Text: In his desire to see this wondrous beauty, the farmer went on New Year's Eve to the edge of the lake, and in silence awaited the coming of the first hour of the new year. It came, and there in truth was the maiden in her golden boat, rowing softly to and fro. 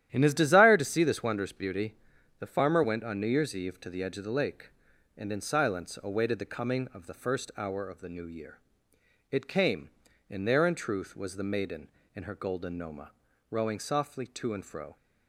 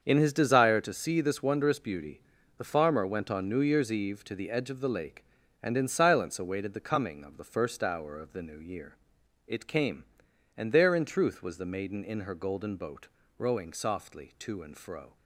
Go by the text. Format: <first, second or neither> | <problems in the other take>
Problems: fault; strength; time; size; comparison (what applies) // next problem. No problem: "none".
second | starts louder than the rest; strong; until 1.1 s; 11.5 dB; also in the second // says "noma" for "boat"; at 12.7 s